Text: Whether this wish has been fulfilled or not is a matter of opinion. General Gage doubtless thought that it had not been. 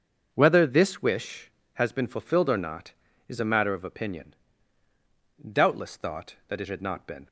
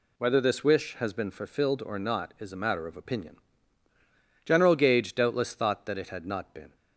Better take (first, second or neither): second